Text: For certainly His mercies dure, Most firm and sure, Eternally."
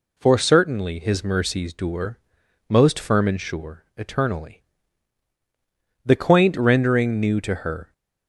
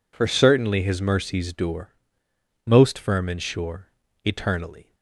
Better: second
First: goes on to say "The quaint rendering new to her"; strong; from 6.0 s on; 1.8 s long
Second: none

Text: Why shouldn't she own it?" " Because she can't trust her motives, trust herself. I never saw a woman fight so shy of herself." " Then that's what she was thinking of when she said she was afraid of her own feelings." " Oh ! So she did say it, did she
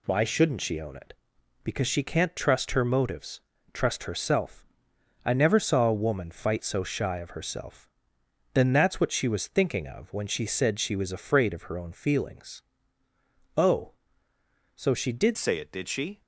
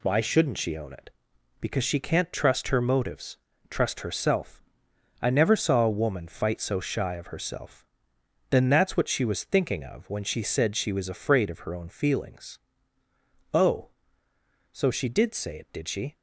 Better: second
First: changes voice at "say"; from 15.3 s on; 0.9 s long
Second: none

